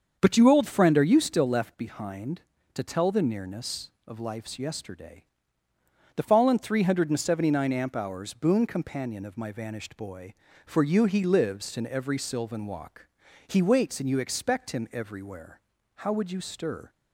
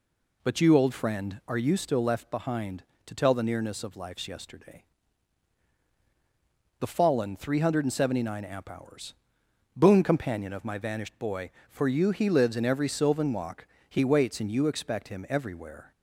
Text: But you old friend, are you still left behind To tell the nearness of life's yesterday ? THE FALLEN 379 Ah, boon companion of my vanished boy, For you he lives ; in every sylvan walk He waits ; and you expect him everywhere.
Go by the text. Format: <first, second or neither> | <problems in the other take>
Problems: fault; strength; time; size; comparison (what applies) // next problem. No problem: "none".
second | starts louder than the rest; until 1.2 s; 7 dB // pauses between "walk" and "He"; at 13.0 s; 0.42 s long; slight in the second // goes on to say "How would you stir"; noticeable; from 15.9 s on; 0.94 s long